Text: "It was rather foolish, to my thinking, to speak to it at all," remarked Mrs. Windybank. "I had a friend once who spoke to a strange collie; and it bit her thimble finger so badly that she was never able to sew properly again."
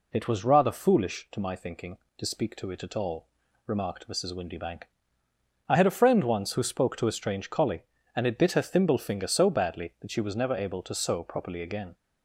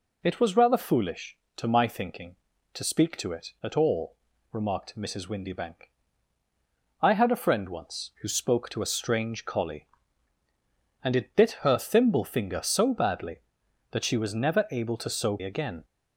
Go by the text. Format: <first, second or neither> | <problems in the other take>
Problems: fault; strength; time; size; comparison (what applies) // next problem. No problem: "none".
first | skips "properly"; at 15.4 s